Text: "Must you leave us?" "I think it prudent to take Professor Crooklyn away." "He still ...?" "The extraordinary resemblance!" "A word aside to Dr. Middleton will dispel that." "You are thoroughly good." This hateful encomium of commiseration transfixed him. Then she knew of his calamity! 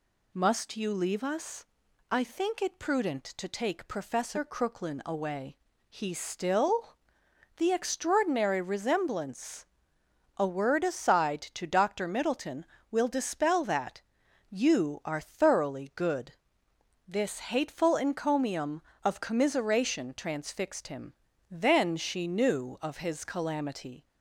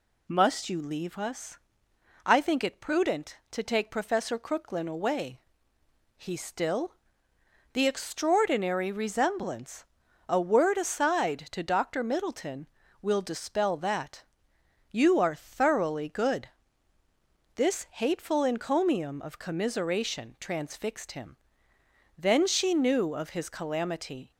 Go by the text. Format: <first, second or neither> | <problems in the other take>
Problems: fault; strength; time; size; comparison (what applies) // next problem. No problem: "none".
neither | none